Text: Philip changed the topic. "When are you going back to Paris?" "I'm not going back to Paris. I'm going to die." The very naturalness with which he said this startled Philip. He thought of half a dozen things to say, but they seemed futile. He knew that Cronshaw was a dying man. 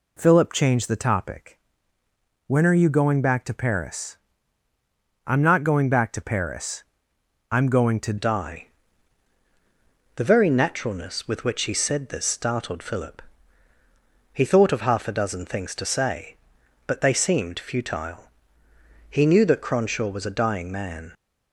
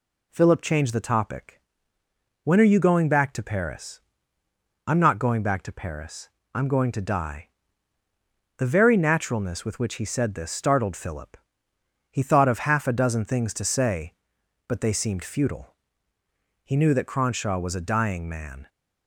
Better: second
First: changes voice at "die"; from 8.1 s on; 13.0 s long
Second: none

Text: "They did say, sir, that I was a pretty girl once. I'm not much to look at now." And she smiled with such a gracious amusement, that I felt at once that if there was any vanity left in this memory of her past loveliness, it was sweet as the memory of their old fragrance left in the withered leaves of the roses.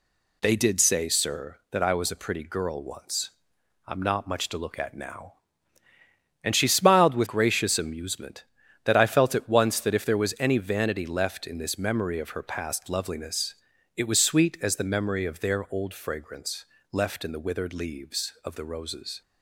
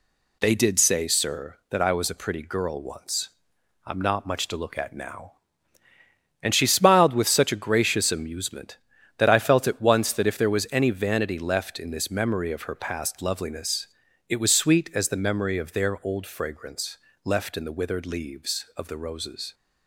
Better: second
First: skips "such a"; at 7.2 s // pauses between "fragrance" and "left"; slight; at 16.6 s; 0.26 s long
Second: pauses between "fragrance" and "left"; slight; at 16.9 s; 0.26 s long

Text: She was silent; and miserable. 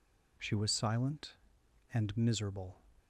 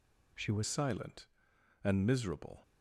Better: first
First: none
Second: changes voice at "silent"; from 0.6 s on; 2.0 s long

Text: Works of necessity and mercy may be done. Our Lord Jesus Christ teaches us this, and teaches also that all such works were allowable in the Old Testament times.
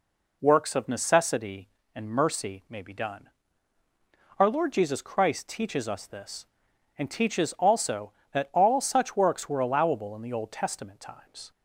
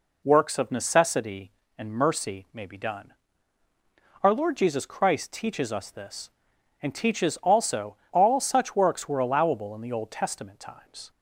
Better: first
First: none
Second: skips "that"; at 8.0 s

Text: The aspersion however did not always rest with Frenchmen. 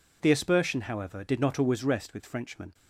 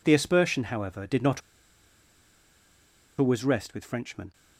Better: first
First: none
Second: pauses between "not" and "always"; strong; at 1.4 s; 1.7 s long

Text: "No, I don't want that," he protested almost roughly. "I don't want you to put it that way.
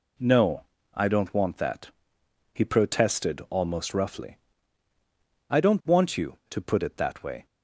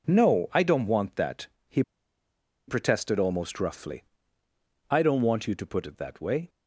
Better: first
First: none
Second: pauses between "he" and "protested"; noticeable; at 1.8 s; 0.86 s long

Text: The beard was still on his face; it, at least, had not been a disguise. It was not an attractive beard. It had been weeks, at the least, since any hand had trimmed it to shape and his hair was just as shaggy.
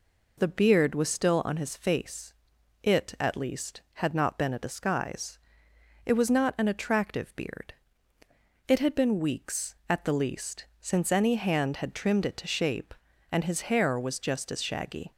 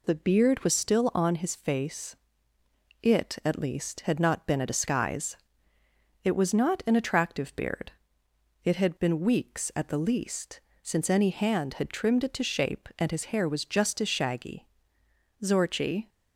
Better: first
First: none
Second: goes on to say "Zorchi"; noticeable; from 15.4 s on; 0.66 s long

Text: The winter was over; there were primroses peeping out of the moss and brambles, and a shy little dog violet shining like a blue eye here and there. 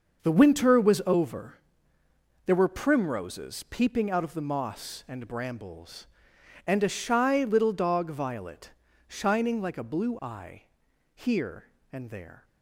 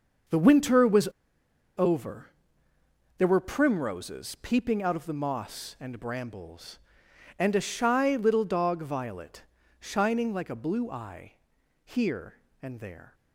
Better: first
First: starts louder than the rest; until 1.2 s; 6.5 dB // pauses between "violet" and "shining"; slight; at 8.7 s; 0.36 s long // pauses between "eye" and "here"; noticeable; at 10.6 s; 0.50 s long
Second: starts louder than the rest; until 2.0 s; 6.5 dB // pauses between "was" and "over"; noticeable; at 1.0 s; 0.71 s long // pauses between "violet" and "shining"; slight; at 9.4 s; 0.36 s long // pauses between "eye" and "here"; noticeable; at 11.3 s; 0.50 s long

